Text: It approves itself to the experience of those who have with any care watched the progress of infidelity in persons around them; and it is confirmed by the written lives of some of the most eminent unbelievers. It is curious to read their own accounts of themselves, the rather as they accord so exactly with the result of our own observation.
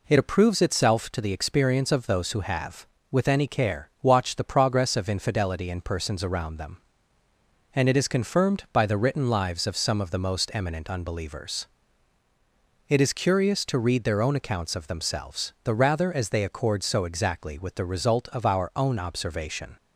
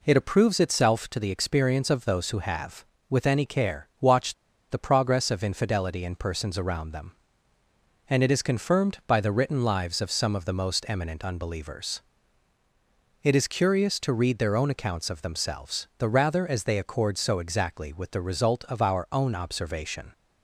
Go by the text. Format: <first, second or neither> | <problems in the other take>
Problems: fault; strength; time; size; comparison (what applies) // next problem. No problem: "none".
first | pauses between "watched" and "the"; at 4.3 s; 0.37 s long